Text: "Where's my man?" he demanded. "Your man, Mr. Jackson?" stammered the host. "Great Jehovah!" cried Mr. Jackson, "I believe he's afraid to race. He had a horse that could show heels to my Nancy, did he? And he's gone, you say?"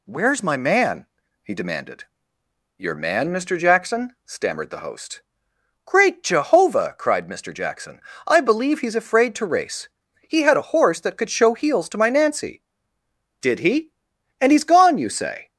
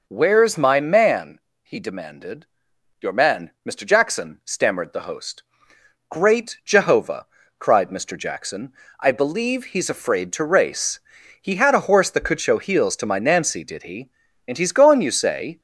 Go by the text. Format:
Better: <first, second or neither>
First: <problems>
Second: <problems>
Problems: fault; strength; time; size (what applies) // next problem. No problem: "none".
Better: neither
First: none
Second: none